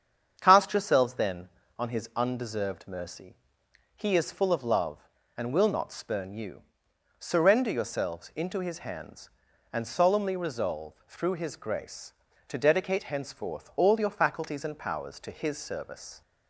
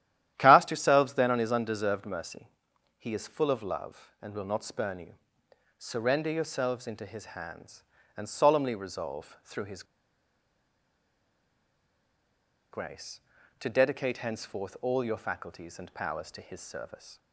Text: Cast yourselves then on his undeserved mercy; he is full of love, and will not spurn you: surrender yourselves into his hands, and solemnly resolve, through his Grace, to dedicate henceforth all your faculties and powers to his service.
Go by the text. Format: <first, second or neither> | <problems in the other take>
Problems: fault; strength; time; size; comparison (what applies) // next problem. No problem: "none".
first | starts louder than the rest; strong; until 1.3 s; 12 dB; strong in the first // pauses between "his" and "Grace"; strong; at 9.8 s; 2.8 s long